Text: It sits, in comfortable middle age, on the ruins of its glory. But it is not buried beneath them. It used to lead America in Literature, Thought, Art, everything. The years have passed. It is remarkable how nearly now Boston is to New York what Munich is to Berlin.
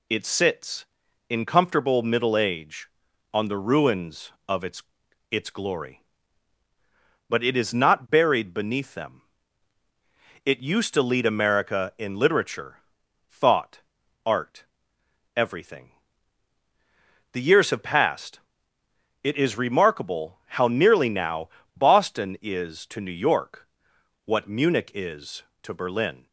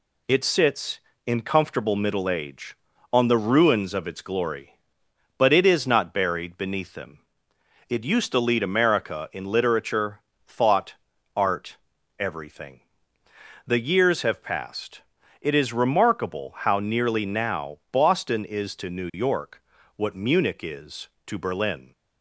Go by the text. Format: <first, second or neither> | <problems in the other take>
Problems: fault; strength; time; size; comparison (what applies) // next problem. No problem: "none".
second | says "its" twice; at 5.3 s // pauses between "now" and "Boston"; slight; at 21.4 s; 0.28 s long // pauses between "York" and "what"; noticeable; at 23.6 s; 0.58 s long; slight in the second